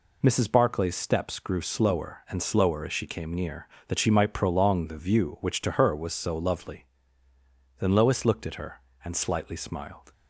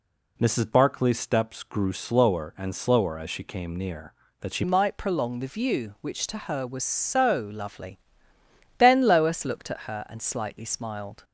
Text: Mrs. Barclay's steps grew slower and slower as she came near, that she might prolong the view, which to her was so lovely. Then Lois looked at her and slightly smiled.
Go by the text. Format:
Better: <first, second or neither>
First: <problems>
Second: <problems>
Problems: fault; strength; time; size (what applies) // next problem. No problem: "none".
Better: first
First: none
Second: changes voice at "might"; from 4.6 s on; 6.6 s long